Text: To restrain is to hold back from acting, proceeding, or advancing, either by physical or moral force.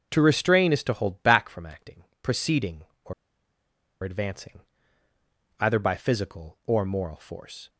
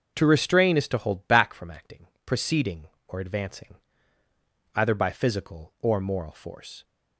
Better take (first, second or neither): second